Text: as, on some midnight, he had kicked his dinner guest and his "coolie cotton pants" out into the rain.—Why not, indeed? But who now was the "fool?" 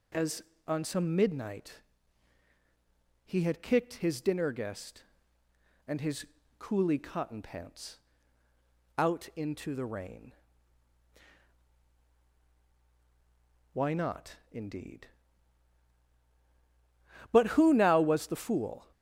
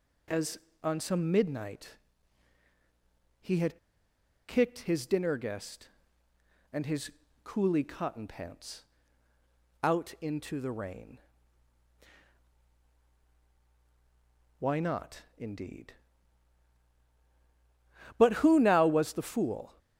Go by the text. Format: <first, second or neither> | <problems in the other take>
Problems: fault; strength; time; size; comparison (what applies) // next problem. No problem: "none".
first | pauses between "had" and "kicked"; noticeable; at 3.7 s; 0.71 s long // pauses between "his" and "coolie"; slight; at 7.1 s; 0.34 s long; slight in the first // pauses between "pants" and "out"; noticeable; at 8.8 s; 0.98 s long; noticeable in the first